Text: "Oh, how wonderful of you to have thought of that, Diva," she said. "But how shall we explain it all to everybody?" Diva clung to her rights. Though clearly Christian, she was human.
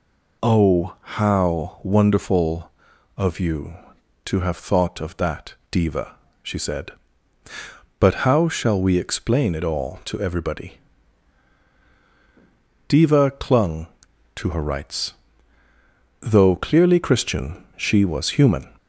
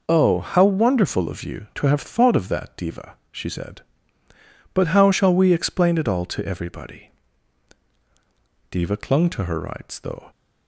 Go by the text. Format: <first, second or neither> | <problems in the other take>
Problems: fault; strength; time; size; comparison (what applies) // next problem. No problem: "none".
first | stops before "clearly Christian she was human"; at 10.3 s